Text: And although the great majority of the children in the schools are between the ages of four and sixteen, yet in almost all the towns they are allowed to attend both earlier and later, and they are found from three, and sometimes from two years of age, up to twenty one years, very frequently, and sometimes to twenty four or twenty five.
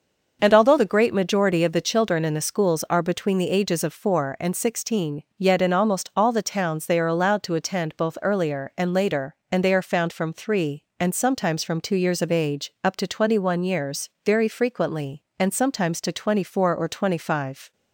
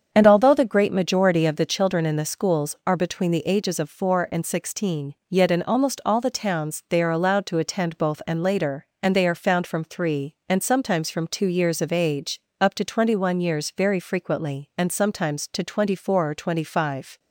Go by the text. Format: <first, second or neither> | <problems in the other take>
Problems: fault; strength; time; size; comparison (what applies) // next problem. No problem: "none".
first | starts louder than the rest; strong; until 1.1 s; 7.5 dB; also in the first // skips "earlier"; at 8.2 s